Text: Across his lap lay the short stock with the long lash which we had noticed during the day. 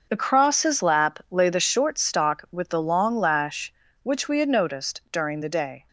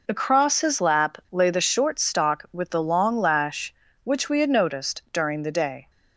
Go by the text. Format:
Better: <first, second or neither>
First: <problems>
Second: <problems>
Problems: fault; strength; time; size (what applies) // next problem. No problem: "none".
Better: second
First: gets quieter; strong; throughout; 12 dB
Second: none